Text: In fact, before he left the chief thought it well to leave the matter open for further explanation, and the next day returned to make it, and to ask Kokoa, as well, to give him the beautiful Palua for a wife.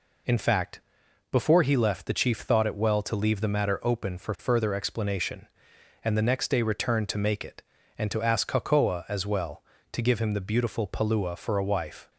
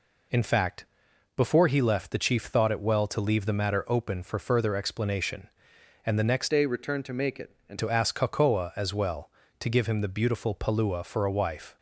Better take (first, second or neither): first